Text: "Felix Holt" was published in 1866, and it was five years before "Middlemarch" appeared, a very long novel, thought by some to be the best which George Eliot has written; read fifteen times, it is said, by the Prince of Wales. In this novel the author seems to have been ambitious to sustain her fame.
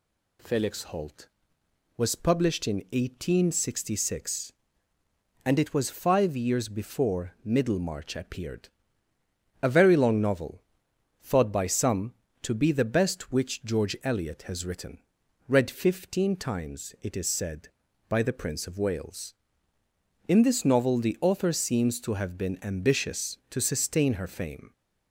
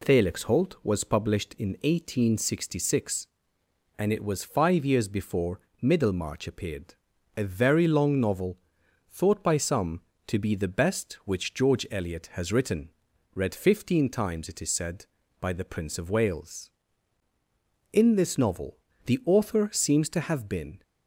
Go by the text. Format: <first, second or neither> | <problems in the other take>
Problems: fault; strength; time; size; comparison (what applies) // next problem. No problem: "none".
first | pauses between "before" and "Middlemarch"; slight; at 5.6 s; 0.20 s long // pauses between "novel" and "the"; slight; at 18.7 s; 0.26 s long // stops before "ambitious to sustain her fame"; at 20.8 s